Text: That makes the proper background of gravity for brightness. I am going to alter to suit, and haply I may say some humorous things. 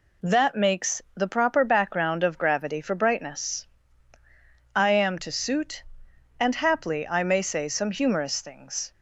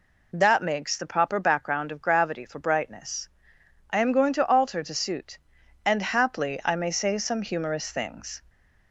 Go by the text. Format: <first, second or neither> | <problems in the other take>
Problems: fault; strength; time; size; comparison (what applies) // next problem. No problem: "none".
second | skips "going to alter"; at 5.1 s